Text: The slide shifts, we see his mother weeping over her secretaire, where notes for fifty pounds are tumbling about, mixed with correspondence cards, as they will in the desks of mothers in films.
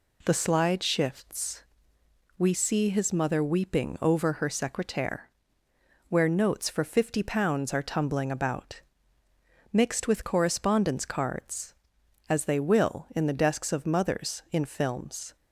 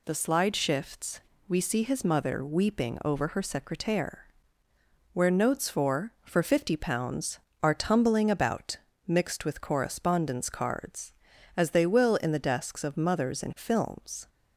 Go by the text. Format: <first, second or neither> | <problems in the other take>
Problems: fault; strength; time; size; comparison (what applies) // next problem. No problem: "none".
first | says "for" twice; at 6.2 s